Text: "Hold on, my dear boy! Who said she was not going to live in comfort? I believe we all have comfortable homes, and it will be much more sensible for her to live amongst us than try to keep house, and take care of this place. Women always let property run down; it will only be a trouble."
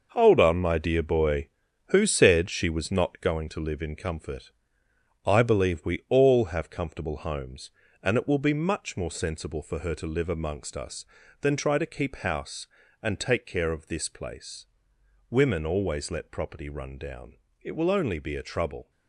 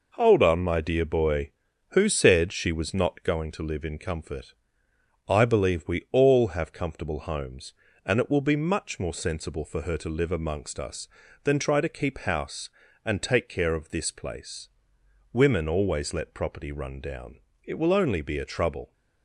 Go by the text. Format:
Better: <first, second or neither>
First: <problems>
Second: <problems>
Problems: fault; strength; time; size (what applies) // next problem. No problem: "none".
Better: second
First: gets quieter; strong; throughout; 9 dB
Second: none